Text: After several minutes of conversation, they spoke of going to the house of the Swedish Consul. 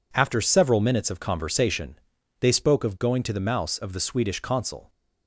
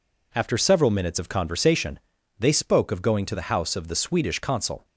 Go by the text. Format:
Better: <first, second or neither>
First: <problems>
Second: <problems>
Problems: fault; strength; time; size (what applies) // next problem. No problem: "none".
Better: second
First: says "mouse" for "house"; at 3.4 s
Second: none